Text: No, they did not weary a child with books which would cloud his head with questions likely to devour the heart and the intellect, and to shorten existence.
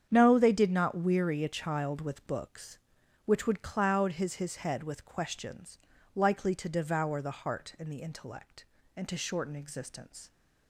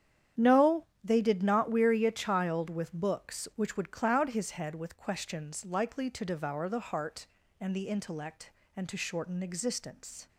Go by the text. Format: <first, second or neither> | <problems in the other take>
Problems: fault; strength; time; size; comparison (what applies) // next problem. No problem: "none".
second | starts louder than the rest; strong; until 1.1 s; 8 dB; strong in the second // says "his" twice; at 4.3 s // pauses between "questions" and "likely"; at 5.7 s; 0.38 s long